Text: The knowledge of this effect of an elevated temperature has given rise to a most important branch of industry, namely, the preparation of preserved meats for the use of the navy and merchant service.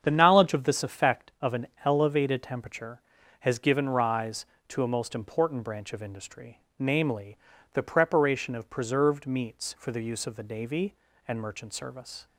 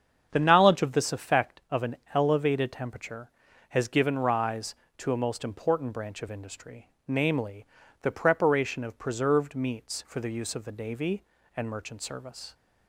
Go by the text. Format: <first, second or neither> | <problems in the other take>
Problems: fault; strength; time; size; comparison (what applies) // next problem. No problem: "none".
neither | starts louder than the rest; strong; the same in both // pauses between "an" and "elevated"; slight; the same in both